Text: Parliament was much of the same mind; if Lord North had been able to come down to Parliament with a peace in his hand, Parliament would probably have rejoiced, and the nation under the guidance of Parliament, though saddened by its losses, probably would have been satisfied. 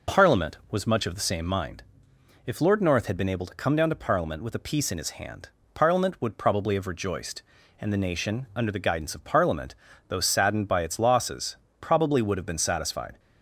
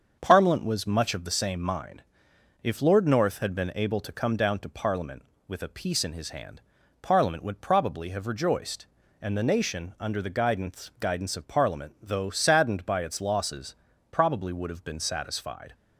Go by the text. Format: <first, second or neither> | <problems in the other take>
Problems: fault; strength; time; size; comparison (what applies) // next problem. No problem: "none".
first | starts louder than the rest; until 1.2 s; 7 dB // says "guidance" twice; at 10.9 s